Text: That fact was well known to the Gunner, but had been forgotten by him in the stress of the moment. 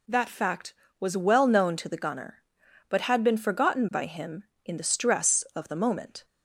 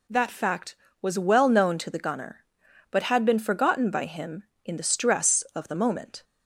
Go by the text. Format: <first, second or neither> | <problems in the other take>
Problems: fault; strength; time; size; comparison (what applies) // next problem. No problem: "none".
neither | none